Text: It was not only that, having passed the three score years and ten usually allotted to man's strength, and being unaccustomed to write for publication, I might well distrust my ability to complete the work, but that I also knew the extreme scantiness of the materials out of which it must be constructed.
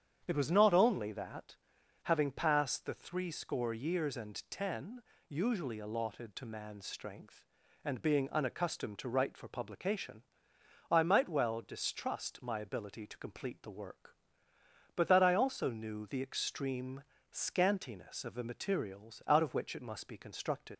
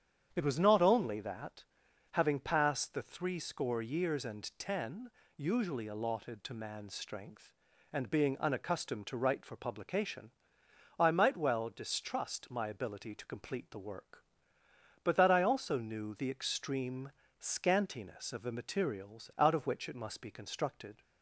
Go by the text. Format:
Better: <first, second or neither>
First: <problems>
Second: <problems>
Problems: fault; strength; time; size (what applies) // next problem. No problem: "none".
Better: second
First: starts louder than the rest; strong; until 1.2 s; 8.5 dB // pauses between "ten" and "usually"; slight; at 5.0 s; 0.26 s long // pauses between "extreme" and "scantiness"; slight; at 17.0 s; 0.28 s long // leaves "constructed" unfinished; at 20.7 s; 135 ms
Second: starts louder than the rest; strong; until 1.3 s; 8.5 dB // pauses between "ten" and "usually"; slight; at 5.0 s; 0.26 s long // pauses between "extreme" and "scantiness"; slight; at 17.1 s; 0.28 s long